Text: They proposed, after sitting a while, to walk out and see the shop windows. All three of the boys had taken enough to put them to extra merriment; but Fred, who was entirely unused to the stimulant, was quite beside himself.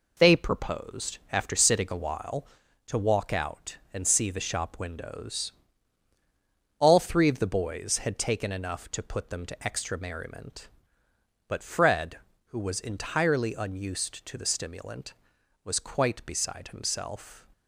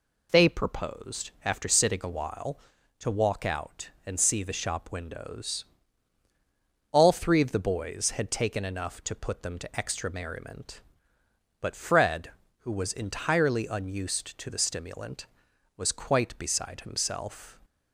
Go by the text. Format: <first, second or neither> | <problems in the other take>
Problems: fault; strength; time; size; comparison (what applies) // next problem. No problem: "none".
second | gets quieter; noticeable; throughout; 6 dB